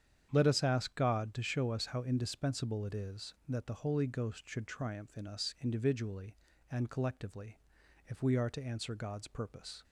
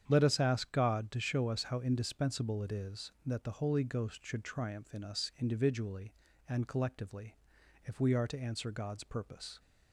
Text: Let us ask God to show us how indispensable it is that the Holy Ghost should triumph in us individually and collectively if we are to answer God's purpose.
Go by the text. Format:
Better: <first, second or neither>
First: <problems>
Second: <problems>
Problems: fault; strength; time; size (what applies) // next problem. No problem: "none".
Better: neither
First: starts louder than the rest; strong; until 1.3 s; 8.5 dB // pauses between "collectively" and "if"; noticeable; at 7.5 s; 0.48 s long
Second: starts louder than the rest; strong; until 1.0 s; 8.5 dB // pauses between "collectively" and "if"; noticeable; at 7.3 s; 0.48 s long